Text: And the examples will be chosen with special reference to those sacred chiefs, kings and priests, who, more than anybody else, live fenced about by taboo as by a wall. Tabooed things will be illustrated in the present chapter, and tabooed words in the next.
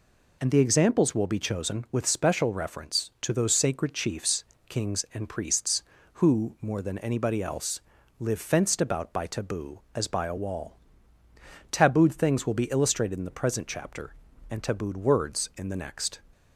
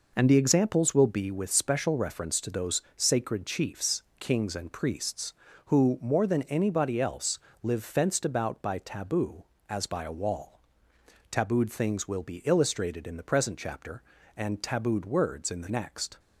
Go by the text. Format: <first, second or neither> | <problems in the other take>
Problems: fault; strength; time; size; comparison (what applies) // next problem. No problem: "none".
first | skips "chosen"; at 1.3 s